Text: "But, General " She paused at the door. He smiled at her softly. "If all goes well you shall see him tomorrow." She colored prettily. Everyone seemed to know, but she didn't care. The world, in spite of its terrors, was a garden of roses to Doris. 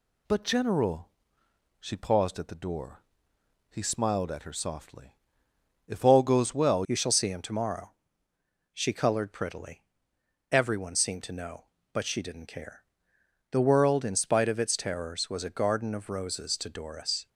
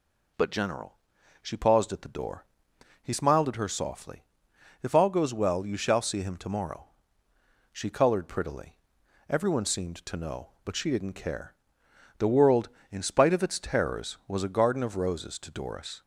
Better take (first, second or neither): second